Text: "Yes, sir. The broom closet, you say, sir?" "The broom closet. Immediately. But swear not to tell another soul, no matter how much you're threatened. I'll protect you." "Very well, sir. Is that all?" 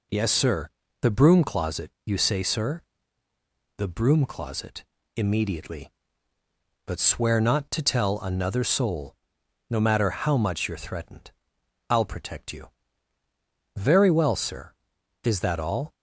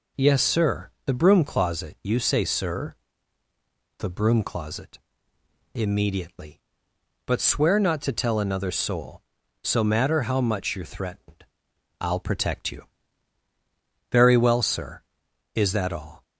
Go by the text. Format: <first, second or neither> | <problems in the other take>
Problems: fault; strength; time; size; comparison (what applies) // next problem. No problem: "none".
first | says "so" for "no"; at 9.6 s